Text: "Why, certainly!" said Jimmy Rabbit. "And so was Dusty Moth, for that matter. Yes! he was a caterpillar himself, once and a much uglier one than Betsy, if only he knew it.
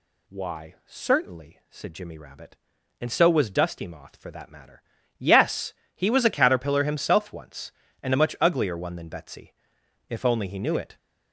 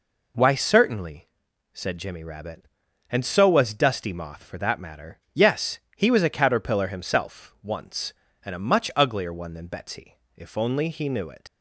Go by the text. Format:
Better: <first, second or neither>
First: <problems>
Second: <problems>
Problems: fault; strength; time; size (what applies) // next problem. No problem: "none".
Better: first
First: none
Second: leaves "it" unfinished; at 11.4 s; 80 ms